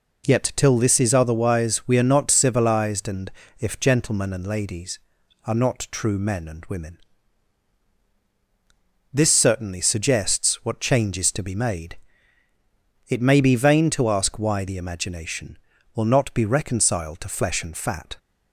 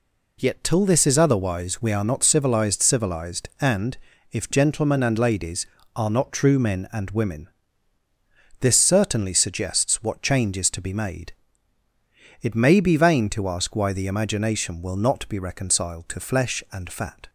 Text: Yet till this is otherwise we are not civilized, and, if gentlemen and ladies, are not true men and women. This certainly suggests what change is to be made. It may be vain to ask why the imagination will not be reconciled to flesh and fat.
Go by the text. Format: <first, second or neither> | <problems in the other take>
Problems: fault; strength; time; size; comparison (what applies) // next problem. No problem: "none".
first | says "civilized" twice; at 2.8 s